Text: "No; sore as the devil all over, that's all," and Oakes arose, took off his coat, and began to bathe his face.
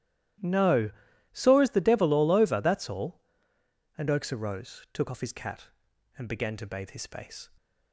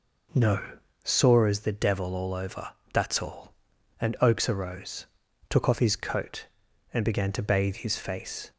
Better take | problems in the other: second | starts louder than the rest; strong; until 1.8 s; 13 dB // says "cat" for "coat"; at 5.3 s

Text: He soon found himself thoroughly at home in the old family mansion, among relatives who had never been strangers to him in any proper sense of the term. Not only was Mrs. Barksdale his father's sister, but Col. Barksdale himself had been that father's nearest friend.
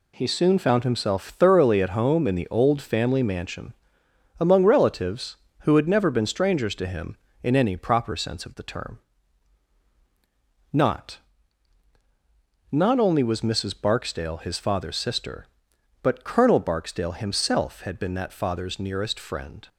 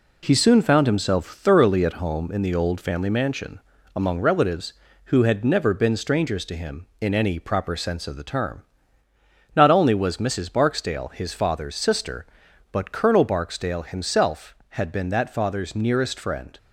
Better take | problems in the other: second | says "Not" twice; at 12.7 s

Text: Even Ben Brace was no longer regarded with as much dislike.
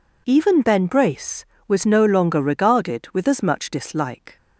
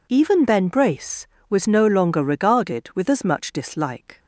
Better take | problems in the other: neither | none

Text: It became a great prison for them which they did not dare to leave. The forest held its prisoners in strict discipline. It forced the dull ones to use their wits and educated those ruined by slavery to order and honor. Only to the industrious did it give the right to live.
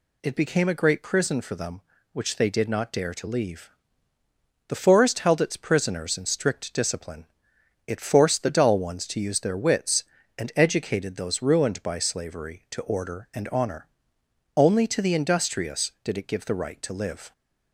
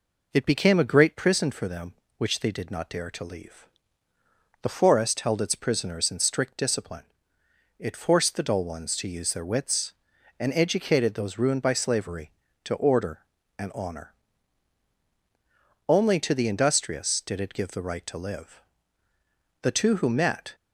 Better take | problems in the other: first | goes on to say "The two who met"; noticeable; from 19.6 s on; 0.94 s long

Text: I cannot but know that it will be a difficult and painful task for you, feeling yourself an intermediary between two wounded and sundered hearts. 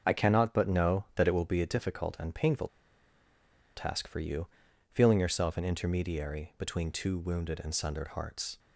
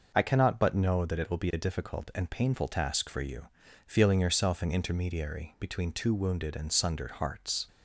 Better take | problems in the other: second | starts louder than the rest; until 1.1 s; 6.5 dB // pauses between "painful" and "task"; at 2.6 s; 1.0 s long

